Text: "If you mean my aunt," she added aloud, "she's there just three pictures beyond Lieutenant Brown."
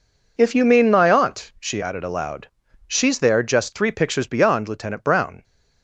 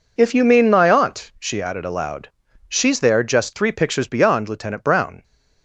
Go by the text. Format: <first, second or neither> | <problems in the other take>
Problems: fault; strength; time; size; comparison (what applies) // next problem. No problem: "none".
neither | none